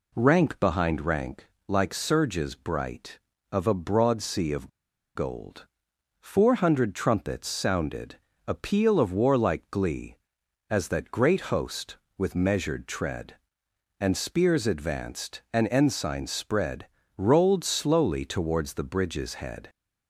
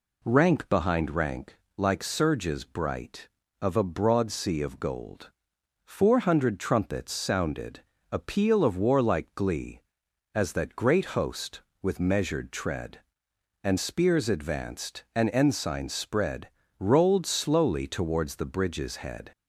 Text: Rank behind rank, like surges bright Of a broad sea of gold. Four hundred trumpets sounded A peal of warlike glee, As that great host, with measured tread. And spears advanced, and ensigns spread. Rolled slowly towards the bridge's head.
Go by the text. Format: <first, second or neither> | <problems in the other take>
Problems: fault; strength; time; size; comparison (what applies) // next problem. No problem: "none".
second | pauses between "of" and "gold"; noticeable; at 4.6 s; 0.46 s long // pauses between "sounded" and "A"; slight; at 8.1 s; 0.32 s long; slight in the second